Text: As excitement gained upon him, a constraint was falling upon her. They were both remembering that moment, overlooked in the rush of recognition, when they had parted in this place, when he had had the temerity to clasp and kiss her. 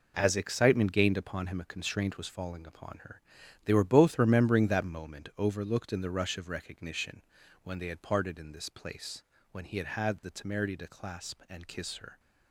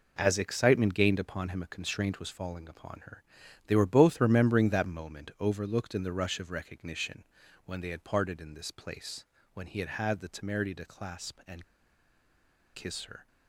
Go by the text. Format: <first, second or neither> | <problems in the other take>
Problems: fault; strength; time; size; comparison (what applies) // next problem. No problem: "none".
first | pauses between "and" and "kiss"; at 11.6 s; 1.1 s long